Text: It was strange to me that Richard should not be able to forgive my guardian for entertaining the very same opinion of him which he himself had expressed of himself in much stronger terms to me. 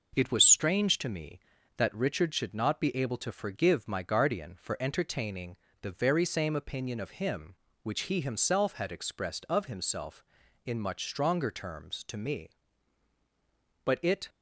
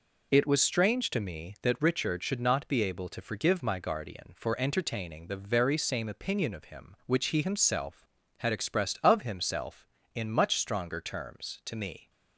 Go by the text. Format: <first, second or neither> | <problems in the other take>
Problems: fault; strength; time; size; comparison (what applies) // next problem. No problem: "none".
second | pauses between "entertaining" and "the"; slight; at 5.5 s; 0.26 s long // goes on to say "But it"; slight; from 13.8 s on; 0.44 s long